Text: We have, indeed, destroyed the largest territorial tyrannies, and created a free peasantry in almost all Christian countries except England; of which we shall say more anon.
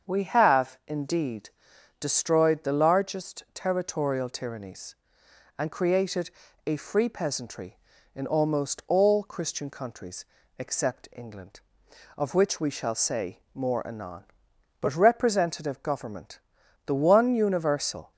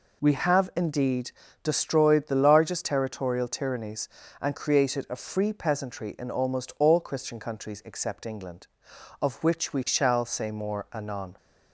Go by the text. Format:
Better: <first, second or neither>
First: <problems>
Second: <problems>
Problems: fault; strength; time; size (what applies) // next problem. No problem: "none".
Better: second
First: starts louder than the rest; until 1.1 s; 7 dB // pauses between "created" and "a"; slight; at 6.3 s; 0.35 s long // pauses between "countries" and "except"; slight; at 10.2 s; 0.32 s long // goes on to say "But representative government the one universal"; strong; from 14.8 s on; 3.3 s long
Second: none